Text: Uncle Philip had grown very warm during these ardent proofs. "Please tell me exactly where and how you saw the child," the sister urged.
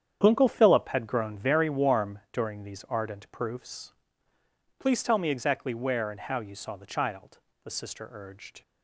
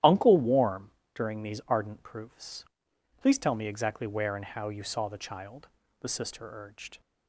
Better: first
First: starts louder than the rest; strong; until 1.2 s; 8.5 dB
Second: starts louder than the rest; strong; until 1.2 s; 12.5 dB // skips "Philip had grown very"; at 0.3 s // pauses between "warm" and "during"; slight; at 0.9 s; 0.26 s long

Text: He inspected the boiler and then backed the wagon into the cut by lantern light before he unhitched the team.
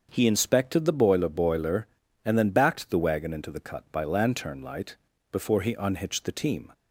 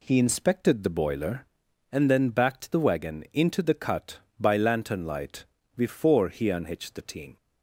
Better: second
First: starts louder than the rest; until 1.1 s; 6.5 dB // says "boiler" twice; at 1.2 s // pauses between "light" and "before"; slight; at 4.9 s; 0.34 s long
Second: pauses between "light" and "before"; slight; at 5.4 s; 0.32 s long

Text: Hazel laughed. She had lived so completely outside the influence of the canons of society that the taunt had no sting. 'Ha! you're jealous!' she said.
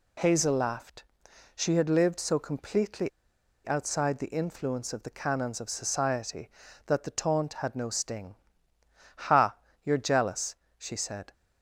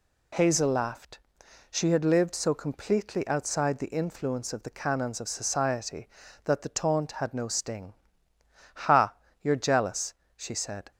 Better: second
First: pauses between "completely" and "outside"; noticeable; at 3.0 s; 0.58 s long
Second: none

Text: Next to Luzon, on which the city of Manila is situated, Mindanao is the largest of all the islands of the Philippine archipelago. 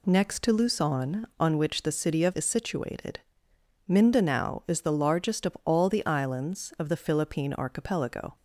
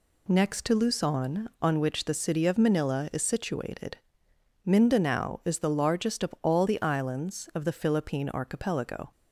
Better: second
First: skips "Manila"; at 2.3 s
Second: none

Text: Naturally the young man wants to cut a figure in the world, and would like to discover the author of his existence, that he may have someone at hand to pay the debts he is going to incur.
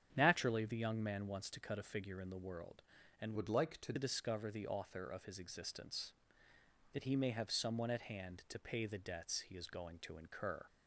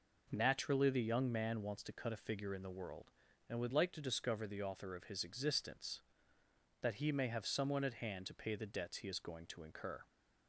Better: second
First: starts louder than the rest; strong; until 1.1 s; 8.5 dB // changes voice from "would" to "to"; from 3.3 to 3.9 s; 0.6 s long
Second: none

